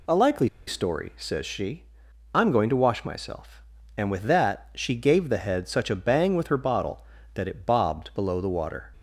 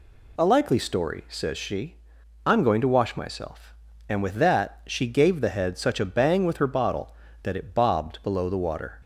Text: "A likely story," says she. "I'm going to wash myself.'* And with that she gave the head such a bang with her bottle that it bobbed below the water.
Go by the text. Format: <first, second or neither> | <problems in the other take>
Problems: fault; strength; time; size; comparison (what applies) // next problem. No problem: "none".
second | pauses between "likely" and "story"; slight; at 0.4 s; 0.19 s long